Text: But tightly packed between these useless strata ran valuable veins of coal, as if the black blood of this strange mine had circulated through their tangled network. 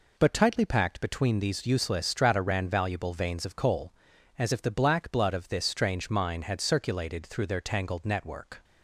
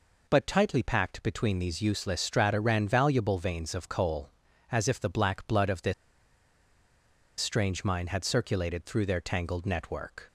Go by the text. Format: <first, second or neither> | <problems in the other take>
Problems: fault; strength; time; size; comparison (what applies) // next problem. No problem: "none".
first | pauses between "this" and "strange"; strong; at 5.9 s; 1.4 s long